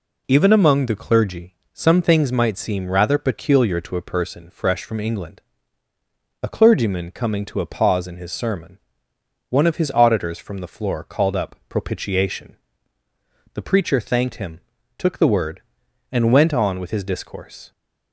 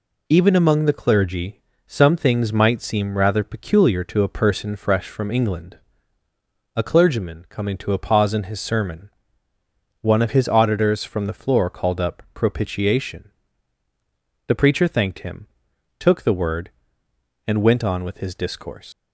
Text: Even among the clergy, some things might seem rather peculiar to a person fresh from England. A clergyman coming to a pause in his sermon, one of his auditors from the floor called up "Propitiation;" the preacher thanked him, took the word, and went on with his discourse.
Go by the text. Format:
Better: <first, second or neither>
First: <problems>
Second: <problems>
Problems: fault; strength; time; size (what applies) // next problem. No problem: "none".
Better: first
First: none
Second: leaves "discourse" unfinished; at 18.9 s; 120 ms